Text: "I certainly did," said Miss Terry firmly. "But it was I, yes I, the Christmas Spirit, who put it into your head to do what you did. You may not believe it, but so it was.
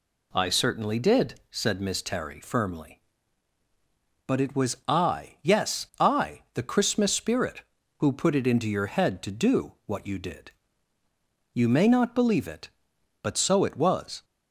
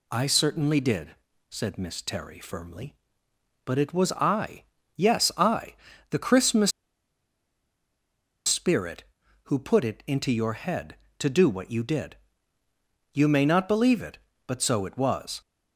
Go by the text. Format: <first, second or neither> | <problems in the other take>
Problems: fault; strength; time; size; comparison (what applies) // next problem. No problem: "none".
first | pauses between "Christmas" and "Spirit"; strong; at 6.7 s; 1.7 s long